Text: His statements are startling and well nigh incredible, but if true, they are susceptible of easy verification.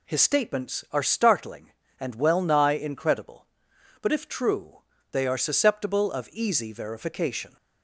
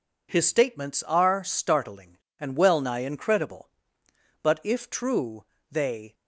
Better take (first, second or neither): first